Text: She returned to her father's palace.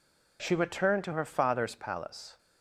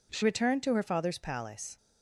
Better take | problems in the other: first | changes voice at "returned"; from 0.2 s on; 1.5 s long

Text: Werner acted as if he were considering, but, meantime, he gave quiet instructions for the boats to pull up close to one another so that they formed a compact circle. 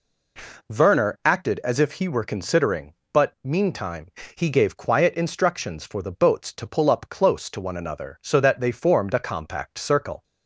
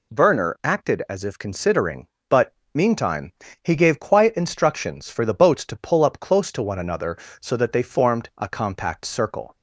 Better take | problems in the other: first | skips "he were"; at 1.3 s

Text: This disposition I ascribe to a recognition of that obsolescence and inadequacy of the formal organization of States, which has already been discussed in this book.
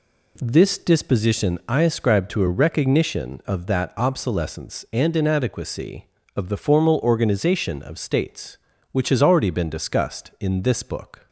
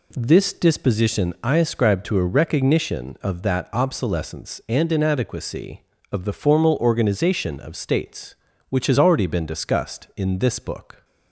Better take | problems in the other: neither | none

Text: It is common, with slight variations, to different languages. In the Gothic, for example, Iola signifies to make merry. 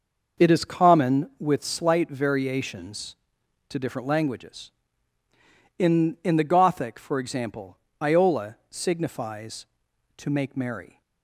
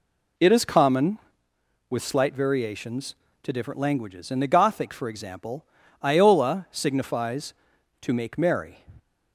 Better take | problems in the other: second | starts louder than the rest; noticeable; until 1.5 s; 6 dB // says "In" twice; at 6.2 s

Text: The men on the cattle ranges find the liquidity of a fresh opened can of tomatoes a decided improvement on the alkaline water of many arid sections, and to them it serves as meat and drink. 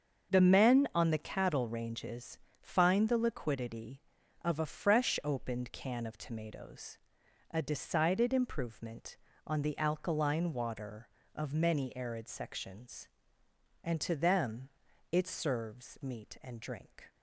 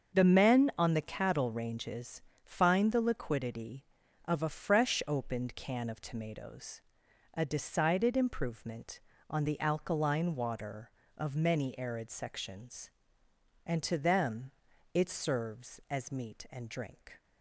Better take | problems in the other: second | starts louder than the rest; until 1.3 s; 6.5 dB; also in the second // pauses between "ranges" and "find"; slight; at 2.3 s; 0.24 s long; slight in the second // pauses between "tomatoes" and "a"; noticeable; at 6.9 s; 0.54 s long; noticeable in the second // pauses between "them" and "it"; at 14.6 s; 0.42 s long; also in the second // skips "as"; at 16.0 s

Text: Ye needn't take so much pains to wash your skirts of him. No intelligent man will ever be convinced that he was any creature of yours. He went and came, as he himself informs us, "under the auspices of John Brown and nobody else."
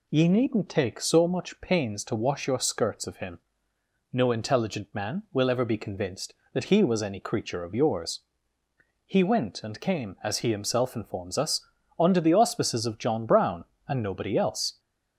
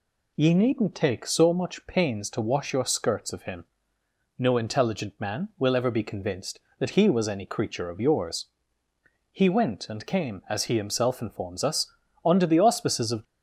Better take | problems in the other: first | stops before "John Brown and nobody else"; at 13.2 s

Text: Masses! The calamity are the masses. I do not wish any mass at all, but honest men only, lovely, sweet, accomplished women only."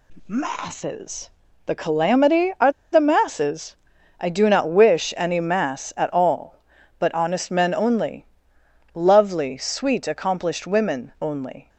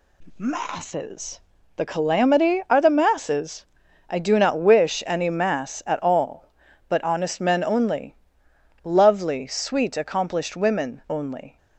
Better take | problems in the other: second | pauses between "are" and "the"; slight; at 2.7 s; 0.20 s long

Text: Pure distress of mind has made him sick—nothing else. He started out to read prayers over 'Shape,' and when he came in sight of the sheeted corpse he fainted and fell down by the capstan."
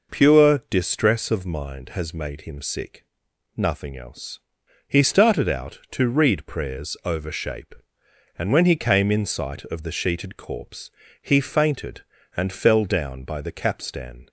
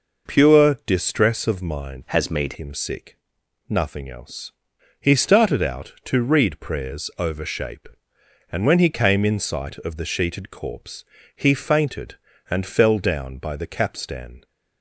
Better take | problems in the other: first | changes voice from "has" to "made"; from 2.0 to 2.5 s; 0.5 s long // pauses between "corpse" and "he"; slight; at 11.0 s; 0.30 s long; slight in the first

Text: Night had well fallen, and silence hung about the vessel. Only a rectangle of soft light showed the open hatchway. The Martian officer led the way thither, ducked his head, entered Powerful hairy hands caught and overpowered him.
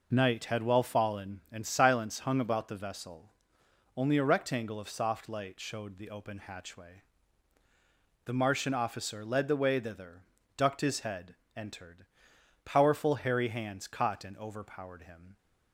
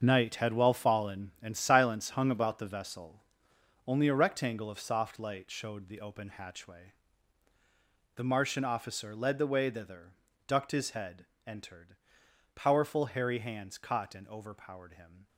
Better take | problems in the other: first | gets quieter; strong; throughout; 11.5 dB // pauses between "entered" and "Powerful"; noticeable; at 11.9 s; 0.62 s long; noticeable in the first

